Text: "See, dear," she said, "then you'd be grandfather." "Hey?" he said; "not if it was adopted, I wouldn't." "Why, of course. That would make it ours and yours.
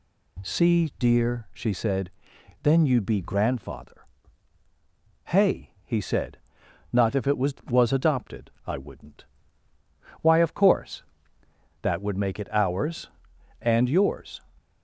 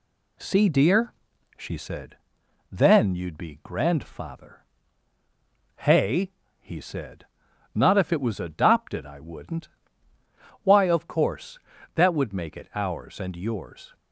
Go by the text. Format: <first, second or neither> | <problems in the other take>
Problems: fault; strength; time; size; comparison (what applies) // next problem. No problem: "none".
second | says "was" twice; at 7.6 s